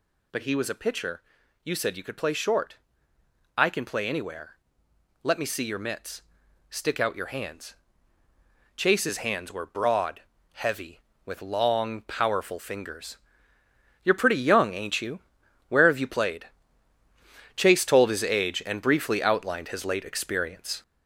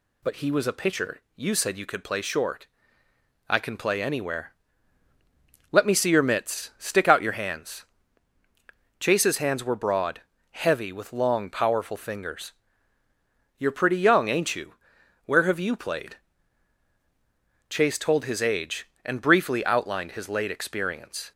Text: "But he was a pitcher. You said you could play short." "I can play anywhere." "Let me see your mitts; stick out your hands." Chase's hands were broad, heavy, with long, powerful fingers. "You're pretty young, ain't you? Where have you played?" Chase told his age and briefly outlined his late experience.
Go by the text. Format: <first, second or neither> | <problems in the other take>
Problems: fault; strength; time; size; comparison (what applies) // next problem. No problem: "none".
second | gets louder; noticeable; throughout; 5 dB